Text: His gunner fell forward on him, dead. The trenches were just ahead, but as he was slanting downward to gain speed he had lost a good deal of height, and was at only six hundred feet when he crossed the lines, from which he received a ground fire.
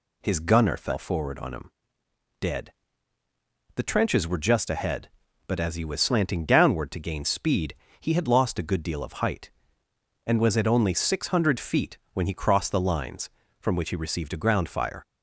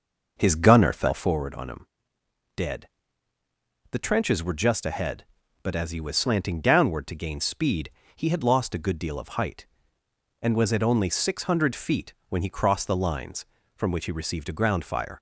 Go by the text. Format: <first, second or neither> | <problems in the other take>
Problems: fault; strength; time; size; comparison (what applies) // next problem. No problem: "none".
first | starts louder than the rest; noticeable; until 1.5 s; 6 dB // pauses between "speed" and "he"; slight; at 7.9 s; 0.24 s long; slight in the first // pauses between "feet" and "when"; slight; at 12.1 s; 0.16 s long; slight in the first